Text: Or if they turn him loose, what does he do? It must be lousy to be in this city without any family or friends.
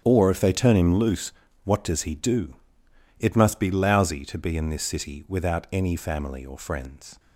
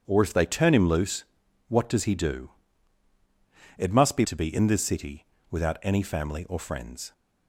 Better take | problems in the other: first | starts louder than the rest; strong; until 1.0 s; 8 dB; strong in the first // skips "lousy"; at 4.2 s // pauses between "city" and "without"; slight; at 5.2 s; 0.26 s long

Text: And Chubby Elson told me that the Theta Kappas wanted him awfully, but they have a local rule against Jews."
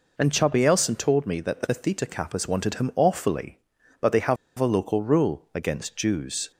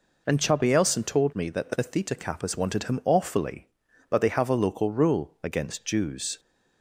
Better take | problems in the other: second | pauses between "have" and "a"; slight; at 4.3 s; 0.22 s long

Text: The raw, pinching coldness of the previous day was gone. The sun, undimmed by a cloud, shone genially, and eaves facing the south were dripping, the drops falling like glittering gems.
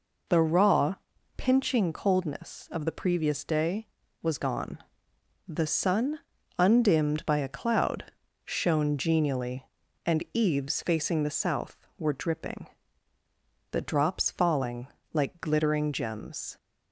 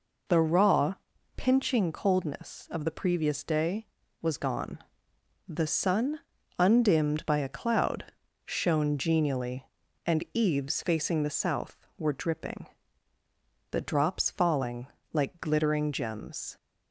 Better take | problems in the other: neither | pauses between "falling" and "like"; slight; the same in both

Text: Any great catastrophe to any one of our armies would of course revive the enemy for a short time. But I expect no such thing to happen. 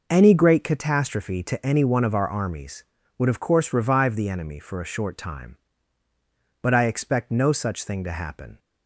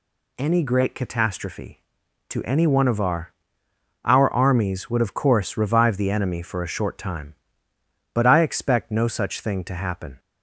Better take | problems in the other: first | says "our" twice; at 4.0 s

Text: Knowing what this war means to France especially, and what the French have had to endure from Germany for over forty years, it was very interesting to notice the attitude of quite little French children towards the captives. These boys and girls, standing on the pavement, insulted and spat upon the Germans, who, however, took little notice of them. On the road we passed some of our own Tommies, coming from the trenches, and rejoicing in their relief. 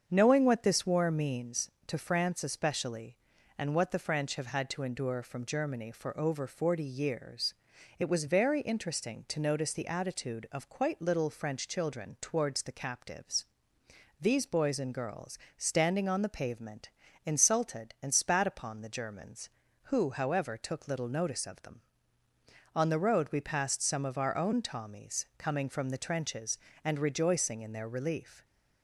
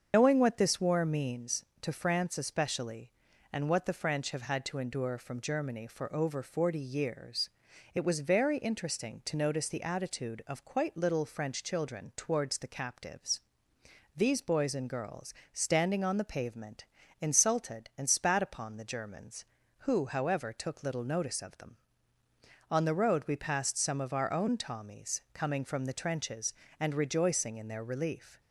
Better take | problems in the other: first | loses the start of "Knowing"; at 0.1 s; 110 ms // starts louder than the rest; until 1.1 s; 7 dB; also in the first

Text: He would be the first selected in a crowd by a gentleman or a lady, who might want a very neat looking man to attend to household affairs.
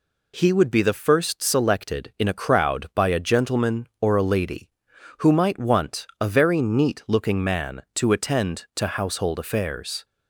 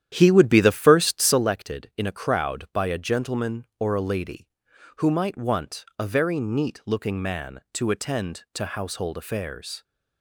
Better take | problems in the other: first | starts louder than the rest; strong; until 1.5 s; 10.5 dB

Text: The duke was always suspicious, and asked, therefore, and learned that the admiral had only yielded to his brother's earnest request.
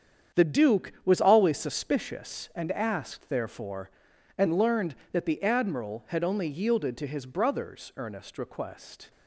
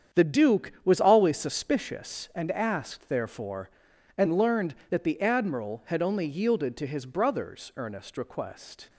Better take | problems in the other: neither | starts louder than the rest; strong; the same in both

